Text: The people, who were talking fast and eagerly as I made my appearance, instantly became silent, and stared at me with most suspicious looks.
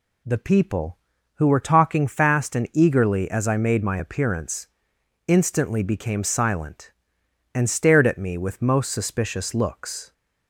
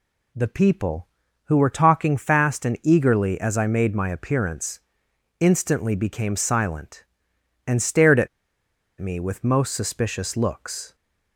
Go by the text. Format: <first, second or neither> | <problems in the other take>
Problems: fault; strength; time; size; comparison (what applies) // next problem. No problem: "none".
first | pauses between "at" and "me"; noticeable; at 8.2 s; 0.72 s long